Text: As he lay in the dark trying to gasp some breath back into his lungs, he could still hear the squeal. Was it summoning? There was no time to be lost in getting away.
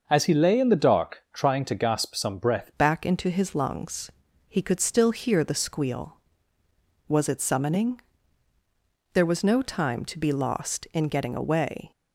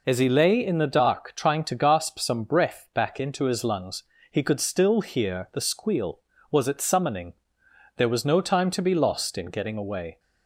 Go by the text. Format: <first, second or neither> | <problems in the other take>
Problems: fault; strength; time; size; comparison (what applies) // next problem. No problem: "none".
second | starts louder than the rest; noticeable; until 1.0 s; 6 dB // changes voice at "back"; from 2.7 s on; 9.2 s long